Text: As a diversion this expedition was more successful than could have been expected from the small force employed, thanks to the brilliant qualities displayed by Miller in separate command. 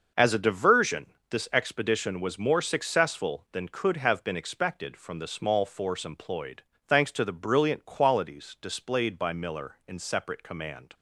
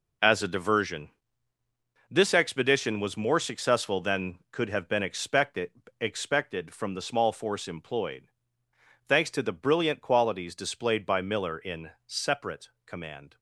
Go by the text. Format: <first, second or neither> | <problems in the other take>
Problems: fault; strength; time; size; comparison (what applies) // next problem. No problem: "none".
first | pauses between "diversion" and "this"; at 1.0 s; 1.0 s long; slight in the first // says "expected" twice; at 5.9 s // pauses between "in" and "separate"; slight; at 11.8 s; 0.18 s long // pauses between "separate" and "command"; slight; at 12.6 s; 0.16 s long